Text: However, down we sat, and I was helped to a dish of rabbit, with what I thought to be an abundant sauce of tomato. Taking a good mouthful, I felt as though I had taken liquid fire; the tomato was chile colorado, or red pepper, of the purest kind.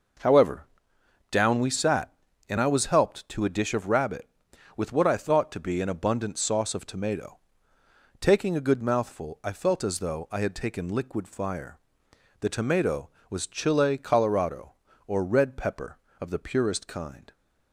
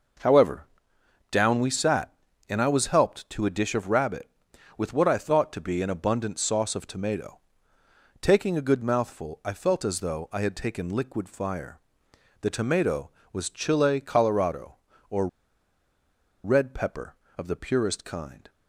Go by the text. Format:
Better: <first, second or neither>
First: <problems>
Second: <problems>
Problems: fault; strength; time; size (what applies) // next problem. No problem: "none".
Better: first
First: none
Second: pauses between "or" and "red"; at 15.2 s; 1.1 s long